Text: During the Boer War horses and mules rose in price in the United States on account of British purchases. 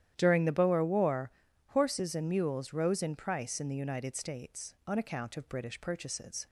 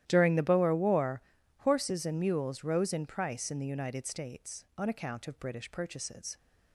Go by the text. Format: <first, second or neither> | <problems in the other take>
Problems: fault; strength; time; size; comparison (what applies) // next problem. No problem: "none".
first | gets quieter; strong; throughout; 20 dB // starts louder than the rest; strong; until 1.0 s; 12.5 dB; strong in the first // pauses between "War" and "horses"; at 1.1 s; 0.40 s long; also in the first